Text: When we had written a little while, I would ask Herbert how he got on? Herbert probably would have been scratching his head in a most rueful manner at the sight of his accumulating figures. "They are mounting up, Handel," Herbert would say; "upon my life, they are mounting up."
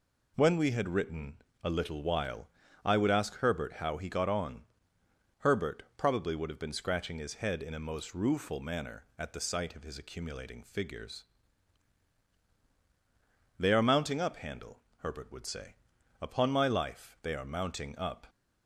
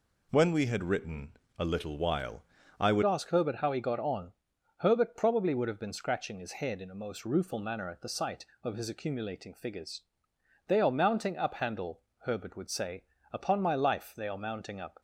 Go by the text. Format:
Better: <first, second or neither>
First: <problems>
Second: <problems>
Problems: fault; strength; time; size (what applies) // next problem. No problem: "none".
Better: first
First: pauses between "written" and "a"; slight; at 1.3 s; 0.26 s long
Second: pauses between "written" and "a"; slight; at 1.3 s; 0.26 s long // changes voice at "ask"; from 3.0 s on; 12.0 s long